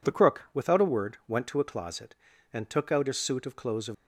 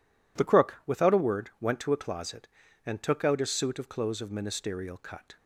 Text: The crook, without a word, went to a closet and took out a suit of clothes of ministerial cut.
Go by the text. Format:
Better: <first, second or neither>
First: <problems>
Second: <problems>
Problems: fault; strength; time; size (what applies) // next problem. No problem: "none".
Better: second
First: stops before "ministerial cut"; at 3.9 s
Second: none